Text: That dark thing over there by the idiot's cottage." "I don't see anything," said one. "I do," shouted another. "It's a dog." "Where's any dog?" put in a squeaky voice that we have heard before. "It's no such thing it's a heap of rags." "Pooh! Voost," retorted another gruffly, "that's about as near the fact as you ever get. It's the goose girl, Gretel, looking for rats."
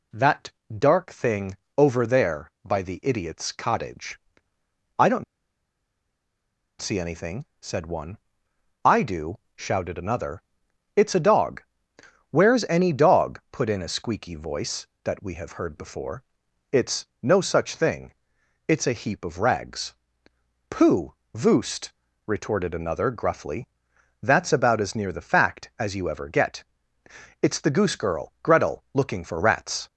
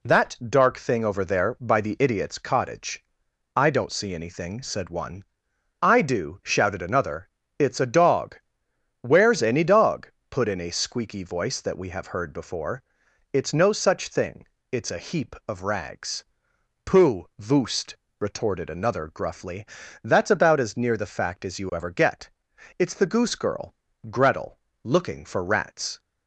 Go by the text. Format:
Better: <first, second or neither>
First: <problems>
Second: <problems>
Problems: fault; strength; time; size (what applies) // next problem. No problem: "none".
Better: second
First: pauses between "That" and "dark"; slight; at 0.5 s; 0.22 s long // pauses between "thing" and "over"; slight; at 1.5 s; 0.18 s long // pauses between "don't" and "see"; strong; at 5.2 s; 1.5 s long // pauses between "thing" and "it's"; noticeable; at 18.1 s; 0.54 s long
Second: pauses between "thing" and "it's"; slight; at 14.4 s; 0.24 s long